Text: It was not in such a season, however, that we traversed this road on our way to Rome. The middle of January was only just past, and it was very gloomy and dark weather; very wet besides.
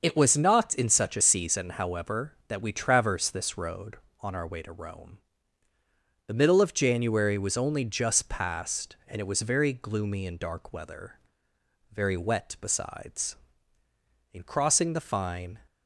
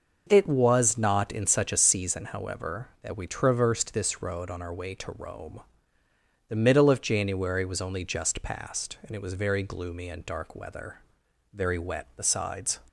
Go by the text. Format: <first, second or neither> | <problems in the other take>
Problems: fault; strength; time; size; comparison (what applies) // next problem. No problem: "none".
second | starts louder than the rest; noticeable; until 1.0 s; 6 dB // goes on to say "In crossing the fine"; noticeable; from 14.3 s on; 1.2 s long